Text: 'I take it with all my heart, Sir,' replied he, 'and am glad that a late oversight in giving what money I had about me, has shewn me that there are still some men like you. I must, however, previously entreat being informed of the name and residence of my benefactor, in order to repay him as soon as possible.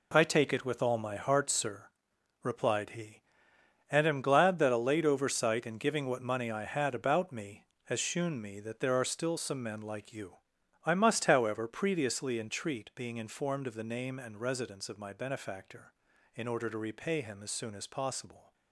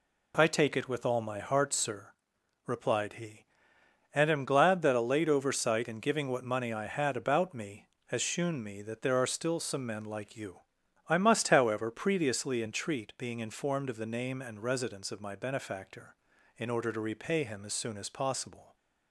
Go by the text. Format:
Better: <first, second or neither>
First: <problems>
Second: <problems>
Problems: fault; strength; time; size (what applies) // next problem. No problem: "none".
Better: second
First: gets quieter; strong; throughout; 10 dB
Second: none